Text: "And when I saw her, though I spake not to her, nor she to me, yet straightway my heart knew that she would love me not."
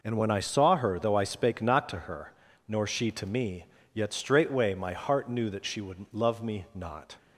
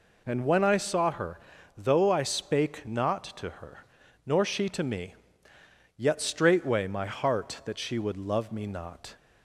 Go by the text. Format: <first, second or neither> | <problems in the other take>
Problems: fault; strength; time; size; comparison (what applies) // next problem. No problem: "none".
first | skips "knew"; at 7.6 s